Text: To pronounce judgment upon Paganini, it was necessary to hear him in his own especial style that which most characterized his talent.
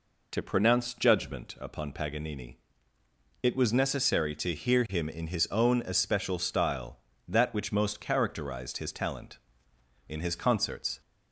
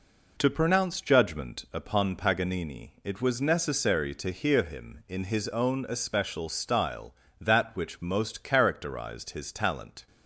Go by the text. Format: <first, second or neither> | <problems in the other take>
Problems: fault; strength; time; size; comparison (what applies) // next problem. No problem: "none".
second | goes on to say "In his concerts"; noticeable; from 10.0 s on; 0.92 s long